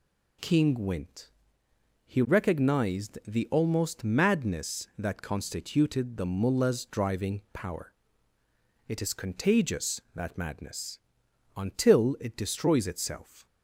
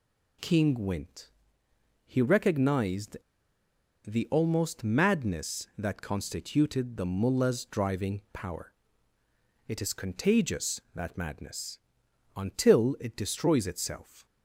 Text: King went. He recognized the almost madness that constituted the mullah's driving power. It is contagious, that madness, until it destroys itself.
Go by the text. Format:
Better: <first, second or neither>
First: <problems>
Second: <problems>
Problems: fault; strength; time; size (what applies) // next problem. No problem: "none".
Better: first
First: none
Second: pauses between "recognized" and "the"; noticeable; at 3.1 s; 0.89 s long